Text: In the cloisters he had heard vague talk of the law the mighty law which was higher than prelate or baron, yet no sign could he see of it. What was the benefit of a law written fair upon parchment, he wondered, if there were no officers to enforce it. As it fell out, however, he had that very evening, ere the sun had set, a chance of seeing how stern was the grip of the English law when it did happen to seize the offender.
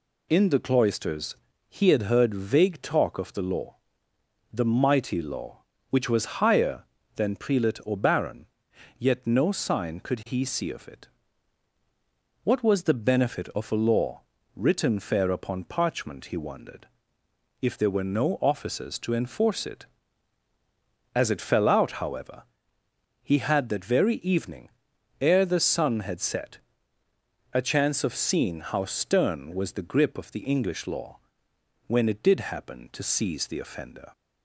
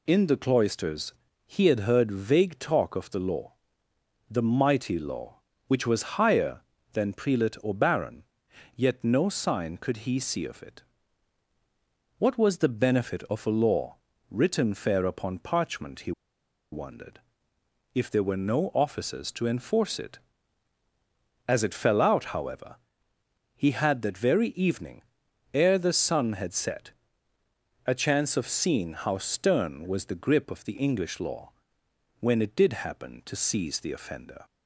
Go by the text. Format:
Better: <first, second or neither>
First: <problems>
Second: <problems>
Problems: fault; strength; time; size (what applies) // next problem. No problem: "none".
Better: first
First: pauses between "cloisters" and "he"; slight; at 1.3 s; 0.32 s long // pauses between "law" and "the"; noticeable; at 3.7 s; 0.74 s long // pauses between "law" and "written"; slight; at 14.2 s; 0.32 s long // pauses between "law" and "when"; noticeable; at 31.1 s; 0.70 s long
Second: pauses between "cloisters" and "he"; slight; at 1.1 s; 0.32 s long // pauses between "law" and "the"; noticeable; at 3.5 s; 0.74 s long // pauses between "law" and "written"; slight; at 13.9 s; 0.32 s long // pauses between "he" and "wondered"; noticeable; at 16.1 s; 0.60 s long // pauses between "law" and "when"; noticeable; at 31.4 s; 0.70 s long